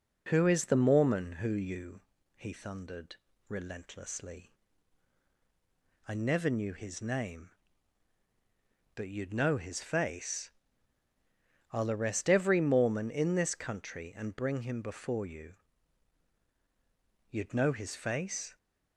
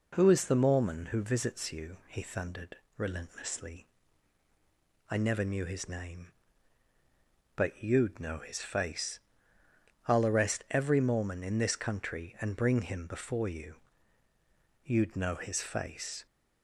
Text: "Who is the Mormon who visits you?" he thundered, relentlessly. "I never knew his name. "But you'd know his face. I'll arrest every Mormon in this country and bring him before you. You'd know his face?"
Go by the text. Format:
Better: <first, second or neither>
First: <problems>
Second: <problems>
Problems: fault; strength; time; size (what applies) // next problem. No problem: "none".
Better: second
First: skips "visits"; at 1.5 s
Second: none